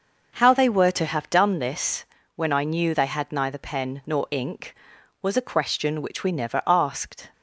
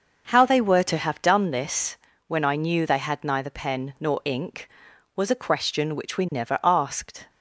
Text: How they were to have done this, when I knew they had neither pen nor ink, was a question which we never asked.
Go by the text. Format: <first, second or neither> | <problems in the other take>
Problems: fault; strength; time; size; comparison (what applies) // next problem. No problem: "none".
neither | starts louder than the rest; the same in both